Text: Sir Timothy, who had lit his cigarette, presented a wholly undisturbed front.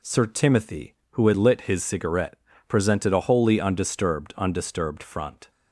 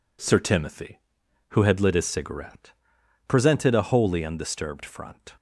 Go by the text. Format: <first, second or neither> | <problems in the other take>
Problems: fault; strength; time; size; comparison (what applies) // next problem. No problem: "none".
second | says "undisturbed" twice; at 4.3 s